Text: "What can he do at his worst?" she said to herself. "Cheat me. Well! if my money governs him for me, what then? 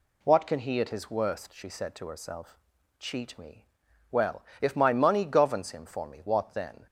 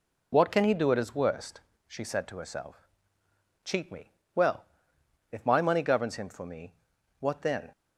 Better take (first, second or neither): second